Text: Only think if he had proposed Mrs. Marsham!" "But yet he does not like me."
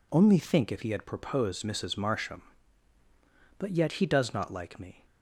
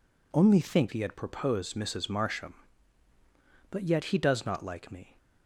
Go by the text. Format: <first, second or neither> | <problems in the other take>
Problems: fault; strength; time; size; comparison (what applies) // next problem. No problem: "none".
first | skips "if"; at 0.9 s